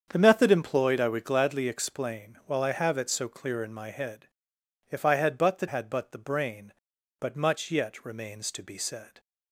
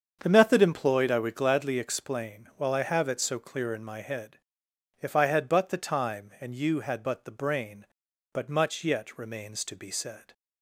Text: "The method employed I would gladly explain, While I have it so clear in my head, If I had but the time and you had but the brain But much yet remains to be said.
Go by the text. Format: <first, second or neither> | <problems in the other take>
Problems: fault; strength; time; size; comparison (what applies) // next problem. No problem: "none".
second | starts louder than the rest; strong; until 1.1 s; 7.5 dB; strong in the second // skips "time and you"; at 5.6 s